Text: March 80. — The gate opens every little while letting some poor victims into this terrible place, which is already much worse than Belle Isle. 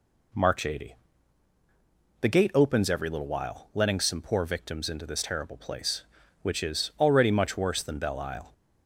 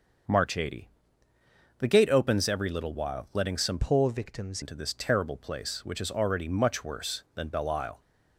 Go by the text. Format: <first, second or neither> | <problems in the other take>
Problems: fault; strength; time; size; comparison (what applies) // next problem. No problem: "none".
first | starts louder than the rest; until 2.1 s; 6.5 dB // changes voice from "poor" to "victims"; from 3.8 to 4.6 s; 0.8 s long